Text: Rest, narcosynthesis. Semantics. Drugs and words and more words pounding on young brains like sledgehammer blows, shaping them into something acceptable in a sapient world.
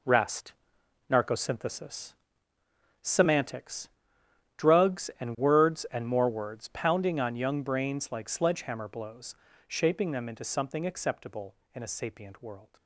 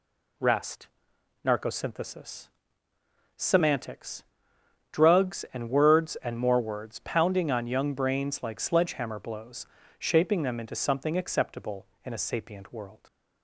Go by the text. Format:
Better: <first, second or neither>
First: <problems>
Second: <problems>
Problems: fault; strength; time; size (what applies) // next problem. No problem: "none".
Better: second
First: gets quieter; strong; throughout; 10 dB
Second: none